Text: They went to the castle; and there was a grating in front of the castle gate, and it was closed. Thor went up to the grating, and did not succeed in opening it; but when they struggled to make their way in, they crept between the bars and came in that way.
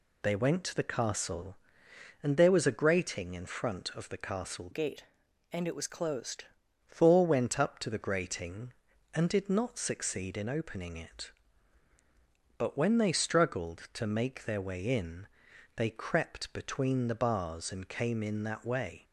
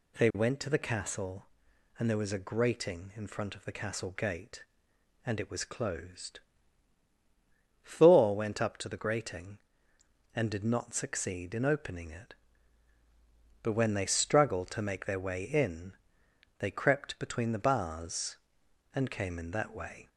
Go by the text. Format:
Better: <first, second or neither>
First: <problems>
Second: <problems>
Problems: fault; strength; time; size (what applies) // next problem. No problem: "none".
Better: second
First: changes voice from "gate" to "closed"; from 4.7 to 6.4 s; 1.7 s long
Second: none